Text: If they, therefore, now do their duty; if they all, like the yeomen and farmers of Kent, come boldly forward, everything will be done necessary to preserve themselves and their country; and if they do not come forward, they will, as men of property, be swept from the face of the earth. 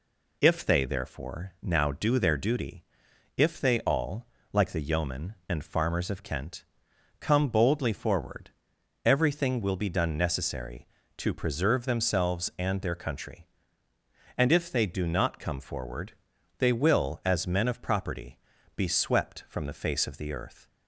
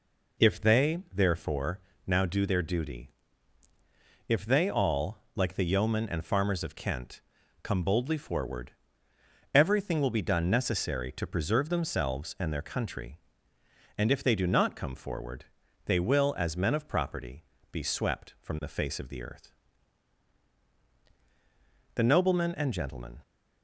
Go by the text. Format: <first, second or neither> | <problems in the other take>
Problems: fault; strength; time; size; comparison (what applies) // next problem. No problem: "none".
first | goes on to say "The noblemen and gentlemen"; noticeable; from 21.9 s on; 1.2 s long